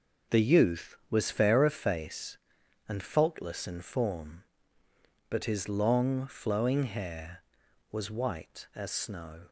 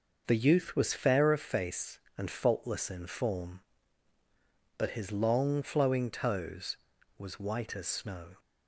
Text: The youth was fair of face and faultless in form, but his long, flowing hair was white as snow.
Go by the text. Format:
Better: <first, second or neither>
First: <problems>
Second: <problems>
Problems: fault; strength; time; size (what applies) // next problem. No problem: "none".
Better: first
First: none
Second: says "toes" for "hair"; at 6.0 s